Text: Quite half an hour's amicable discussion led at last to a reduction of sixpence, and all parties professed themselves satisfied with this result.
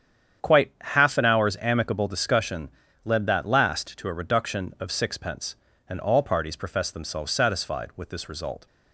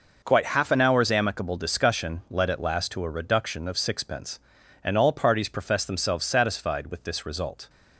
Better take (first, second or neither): second